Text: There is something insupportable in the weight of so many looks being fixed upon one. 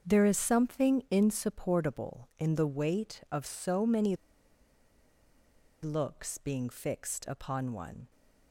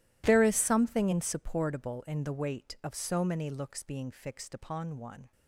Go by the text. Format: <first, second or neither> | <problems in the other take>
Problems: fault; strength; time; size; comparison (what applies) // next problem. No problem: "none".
second | starts louder than the rest; until 1.1 s; 7 dB // pauses between "many" and "looks"; strong; at 4.1 s; 1.6 s long